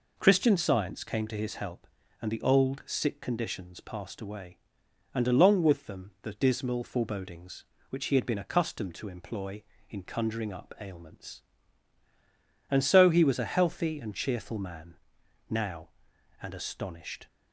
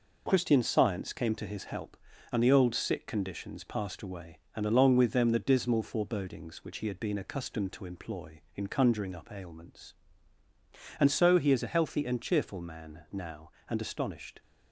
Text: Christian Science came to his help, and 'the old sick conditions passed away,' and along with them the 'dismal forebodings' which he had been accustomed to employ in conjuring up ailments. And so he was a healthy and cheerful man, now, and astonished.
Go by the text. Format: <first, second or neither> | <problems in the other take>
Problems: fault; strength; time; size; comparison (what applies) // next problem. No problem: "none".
first | says "is" for "was"; at 11.5 s